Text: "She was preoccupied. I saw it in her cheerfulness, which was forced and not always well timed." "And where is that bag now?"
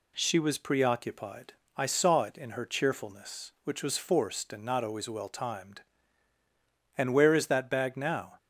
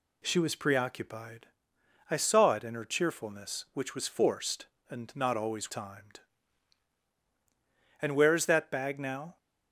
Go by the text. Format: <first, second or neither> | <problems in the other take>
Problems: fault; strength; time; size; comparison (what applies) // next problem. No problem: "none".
first | skips "well"; at 5.7 s